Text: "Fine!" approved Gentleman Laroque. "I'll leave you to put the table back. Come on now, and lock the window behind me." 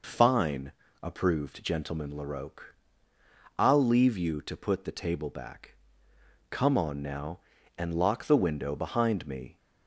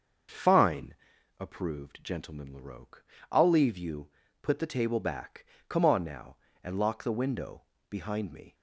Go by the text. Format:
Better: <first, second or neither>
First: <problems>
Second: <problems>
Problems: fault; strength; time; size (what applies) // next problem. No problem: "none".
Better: first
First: none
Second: starts louder than the rest; until 1.7 s; 6.5 dB // skips "to"; at 4.2 s // pauses between "window" and "behind"; slight; at 7.6 s; 0.26 s long